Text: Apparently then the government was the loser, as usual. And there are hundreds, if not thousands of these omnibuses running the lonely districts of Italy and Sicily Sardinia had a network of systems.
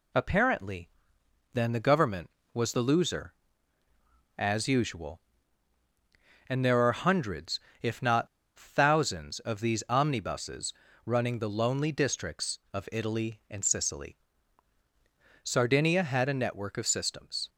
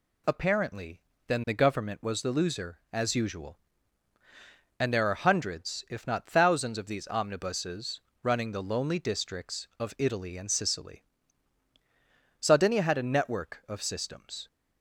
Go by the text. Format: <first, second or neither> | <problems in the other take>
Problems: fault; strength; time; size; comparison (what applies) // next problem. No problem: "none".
second | pauses between "Apparently" and "then"; noticeable; at 0.8 s; 0.64 s long; slight in the second // pauses between "not" and "thousands"; slight; at 8.2 s; 0.31 s long // pauses between "omnibuses" and "running"; slight; at 10.7 s; 0.32 s long; slight in the second // pauses between "Sicily" and "Sardinia"; strong; at 14.1 s; 1.2 s long; strong in the second